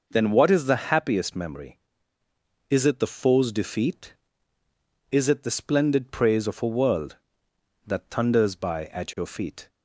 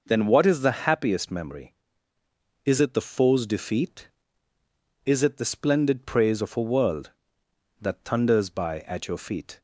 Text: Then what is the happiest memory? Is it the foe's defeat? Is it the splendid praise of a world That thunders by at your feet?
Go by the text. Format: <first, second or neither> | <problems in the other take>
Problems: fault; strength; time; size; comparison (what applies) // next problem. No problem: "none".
neither | none